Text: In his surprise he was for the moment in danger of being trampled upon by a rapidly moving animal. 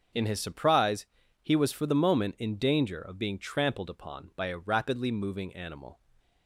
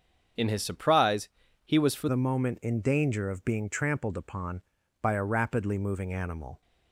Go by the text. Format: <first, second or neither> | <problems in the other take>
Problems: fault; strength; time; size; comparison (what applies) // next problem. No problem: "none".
first | starts louder than the rest; strong; until 1.7 s; 7 dB; also in the first // pauses between "surprise" and "he"; at 1.2 s; 0.38 s long; also in the first // changes voice at "the"; from 2.0 s on; 4.6 s long